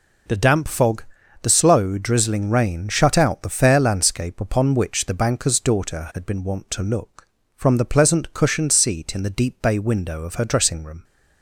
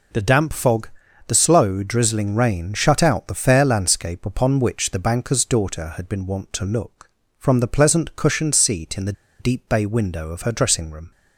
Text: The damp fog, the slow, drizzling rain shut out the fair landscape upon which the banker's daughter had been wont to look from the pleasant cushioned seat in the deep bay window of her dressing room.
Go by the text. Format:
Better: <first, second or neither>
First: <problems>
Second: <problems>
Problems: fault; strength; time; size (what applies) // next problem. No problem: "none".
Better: first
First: none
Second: pauses between "the" and "deep"; slight; at 9.1 s; 0.27 s long